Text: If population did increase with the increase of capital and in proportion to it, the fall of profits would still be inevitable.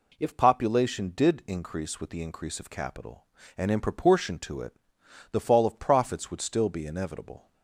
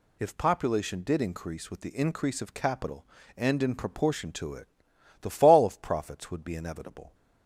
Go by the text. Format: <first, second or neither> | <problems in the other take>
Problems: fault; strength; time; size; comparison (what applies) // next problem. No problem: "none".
first | skips "still"; at 6.4 s